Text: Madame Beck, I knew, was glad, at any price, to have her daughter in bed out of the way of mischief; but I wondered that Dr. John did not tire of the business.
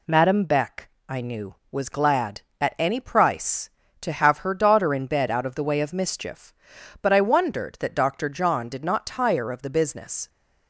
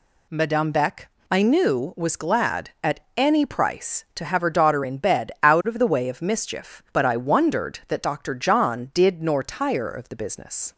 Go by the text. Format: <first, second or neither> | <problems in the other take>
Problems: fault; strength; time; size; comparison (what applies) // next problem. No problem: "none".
first | pauses between "at" and "any"; slight; at 2.9 s; 0.16 s long // says "nor" for "not"; at 9.2 s